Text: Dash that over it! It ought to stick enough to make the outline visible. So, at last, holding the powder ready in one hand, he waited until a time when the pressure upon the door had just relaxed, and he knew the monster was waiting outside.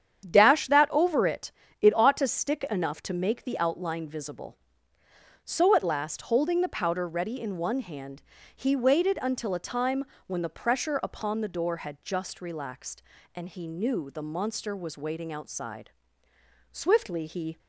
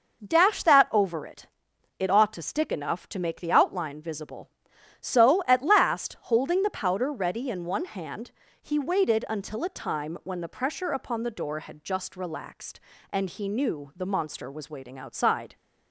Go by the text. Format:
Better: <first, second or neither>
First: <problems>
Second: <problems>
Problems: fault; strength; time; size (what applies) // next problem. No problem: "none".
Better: second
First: starts louder than the rest; strong; until 1.2 s; 8.5 dB // pauses between "time" and "when"; slight; at 10.0 s; 0.20 s long // goes on to say "Swiftly he"; noticeable; from 16.7 s on; 0.86 s long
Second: none